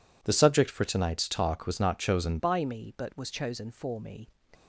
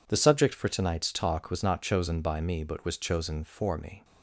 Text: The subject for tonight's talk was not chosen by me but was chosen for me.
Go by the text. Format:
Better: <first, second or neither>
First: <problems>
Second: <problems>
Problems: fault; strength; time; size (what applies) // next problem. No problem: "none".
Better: second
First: changes voice at "by"; from 2.3 s on; 1.9 s long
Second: none